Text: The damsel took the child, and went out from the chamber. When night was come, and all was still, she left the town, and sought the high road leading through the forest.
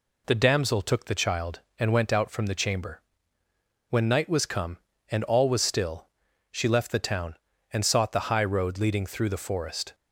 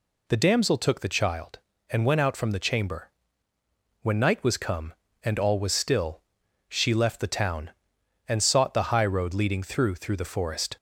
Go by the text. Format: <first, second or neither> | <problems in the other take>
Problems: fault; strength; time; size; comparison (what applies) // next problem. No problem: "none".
first | says "through" twice; at 9.9 s